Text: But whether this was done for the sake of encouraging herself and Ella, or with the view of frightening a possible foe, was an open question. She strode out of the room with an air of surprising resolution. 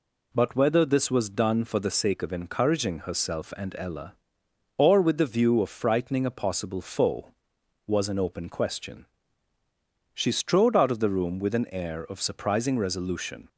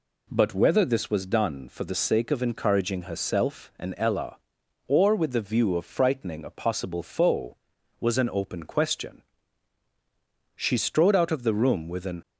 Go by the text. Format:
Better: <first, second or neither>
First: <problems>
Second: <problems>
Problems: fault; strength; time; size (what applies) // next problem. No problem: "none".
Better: first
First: none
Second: stops before "air of surprising resolution"; at 12.2 s